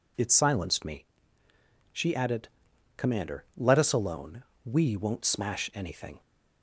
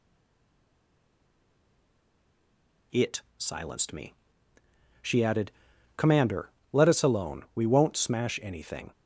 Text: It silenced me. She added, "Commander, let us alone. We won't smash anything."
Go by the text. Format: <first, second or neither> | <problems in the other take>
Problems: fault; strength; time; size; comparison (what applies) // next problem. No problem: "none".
first | stays silent before the first word; strong; until 2.9 s; 2.9 s long